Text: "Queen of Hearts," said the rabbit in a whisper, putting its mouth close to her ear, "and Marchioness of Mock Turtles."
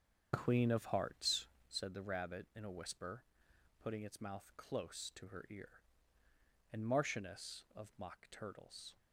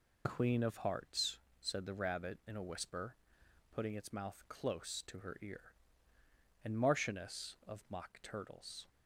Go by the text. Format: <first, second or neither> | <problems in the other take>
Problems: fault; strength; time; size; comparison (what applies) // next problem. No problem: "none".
second | starts louder than the rest; until 1.9 s; 7 dB